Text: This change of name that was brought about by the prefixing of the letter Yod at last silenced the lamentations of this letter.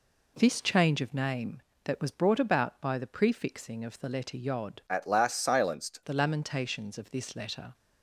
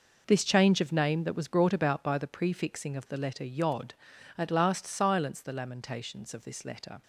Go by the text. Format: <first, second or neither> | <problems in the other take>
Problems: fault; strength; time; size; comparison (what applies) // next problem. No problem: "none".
second | changes voice from "at" to "silenced"; from 4.8 to 5.9 s; 1.1 s long